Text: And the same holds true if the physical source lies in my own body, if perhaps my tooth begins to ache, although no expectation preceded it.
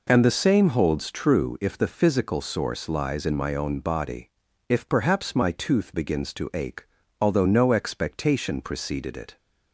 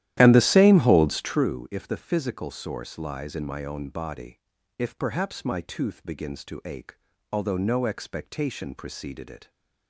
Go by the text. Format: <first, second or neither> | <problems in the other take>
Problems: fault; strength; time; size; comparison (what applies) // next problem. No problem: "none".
first | starts louder than the rest; strong; until 1.4 s; 12.5 dB